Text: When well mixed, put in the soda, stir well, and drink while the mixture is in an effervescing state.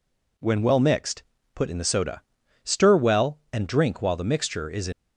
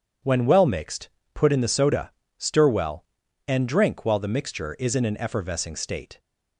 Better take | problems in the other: second | stops before "an effervescing state"; at 4.9 s

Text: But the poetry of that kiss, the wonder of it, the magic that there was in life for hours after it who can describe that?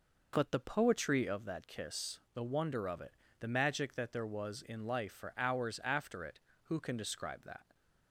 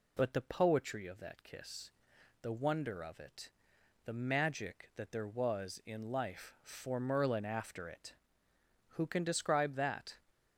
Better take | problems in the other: first | says "merlin" for "hours"; at 6.9 s

